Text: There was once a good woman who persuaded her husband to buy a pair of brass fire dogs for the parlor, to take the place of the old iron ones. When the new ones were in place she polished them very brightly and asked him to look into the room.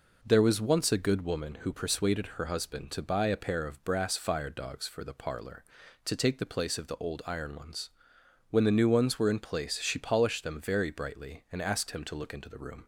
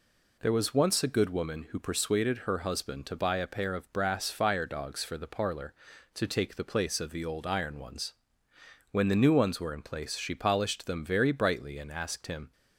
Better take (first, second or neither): first